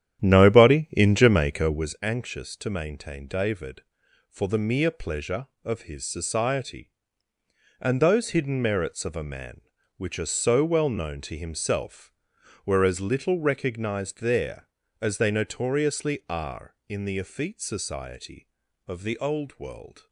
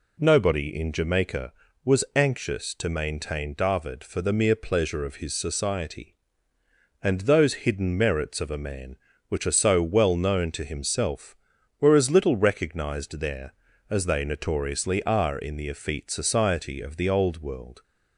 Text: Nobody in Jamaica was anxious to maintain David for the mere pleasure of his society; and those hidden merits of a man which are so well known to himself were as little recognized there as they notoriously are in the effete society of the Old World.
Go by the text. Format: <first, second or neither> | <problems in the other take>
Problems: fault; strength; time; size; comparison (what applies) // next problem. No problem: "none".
second | starts louder than the rest; strong; until 2.0 s; 10.5 dB